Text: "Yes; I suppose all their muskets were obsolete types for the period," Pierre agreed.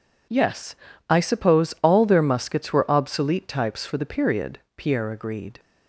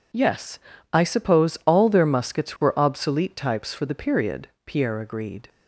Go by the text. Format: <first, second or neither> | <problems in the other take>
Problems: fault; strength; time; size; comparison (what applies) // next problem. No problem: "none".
neither | none